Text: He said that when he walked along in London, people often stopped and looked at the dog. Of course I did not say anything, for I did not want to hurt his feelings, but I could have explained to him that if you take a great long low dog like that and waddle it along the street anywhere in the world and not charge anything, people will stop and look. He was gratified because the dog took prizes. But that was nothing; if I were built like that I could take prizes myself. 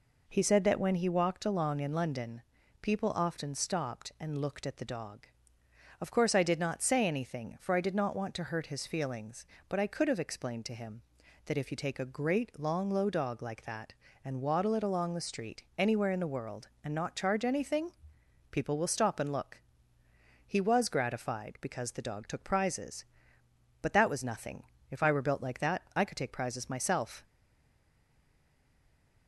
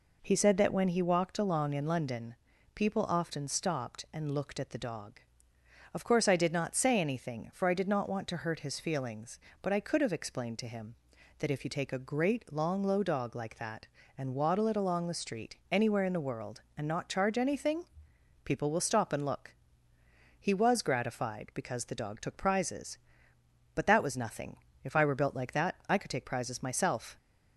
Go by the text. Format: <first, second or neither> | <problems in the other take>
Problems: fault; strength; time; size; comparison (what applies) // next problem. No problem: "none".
second | stays silent after the last word; noticeable; from 27.2 s on; 2.0 s long